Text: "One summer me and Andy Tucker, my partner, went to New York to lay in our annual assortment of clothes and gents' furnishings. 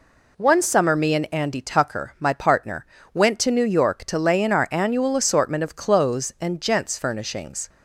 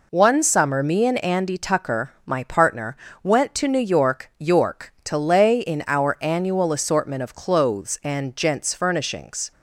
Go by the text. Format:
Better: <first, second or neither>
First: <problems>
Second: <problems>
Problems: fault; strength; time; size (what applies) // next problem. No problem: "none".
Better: first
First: none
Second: says "York" twice; at 4.3 s